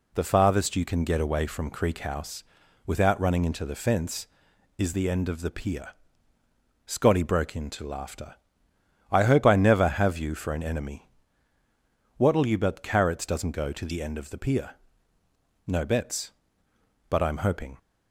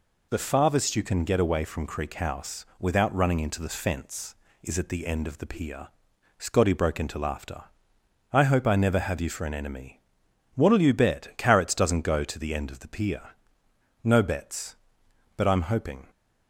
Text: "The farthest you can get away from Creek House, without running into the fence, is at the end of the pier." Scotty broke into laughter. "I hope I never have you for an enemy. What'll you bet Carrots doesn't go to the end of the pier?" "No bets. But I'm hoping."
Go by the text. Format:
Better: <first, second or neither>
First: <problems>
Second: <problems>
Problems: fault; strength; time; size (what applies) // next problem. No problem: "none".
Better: second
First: skips "at"; at 4.9 s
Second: none